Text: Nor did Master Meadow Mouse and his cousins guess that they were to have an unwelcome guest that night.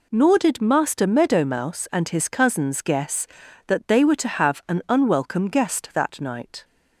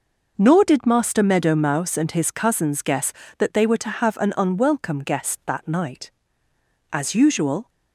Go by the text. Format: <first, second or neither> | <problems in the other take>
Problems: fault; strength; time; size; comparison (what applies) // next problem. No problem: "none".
first | goes on to say "As usual"; noticeable; from 6.9 s on; 0.78 s long